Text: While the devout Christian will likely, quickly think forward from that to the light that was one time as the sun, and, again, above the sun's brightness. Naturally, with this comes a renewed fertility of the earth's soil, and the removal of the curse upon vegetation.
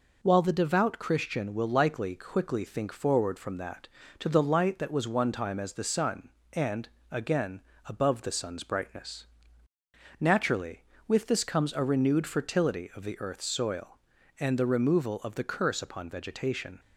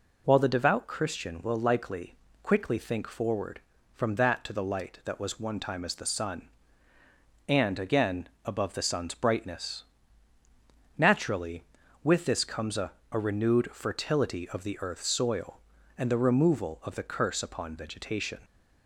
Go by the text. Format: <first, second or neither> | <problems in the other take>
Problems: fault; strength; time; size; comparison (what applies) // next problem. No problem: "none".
first | says "a" twice; at 13.1 s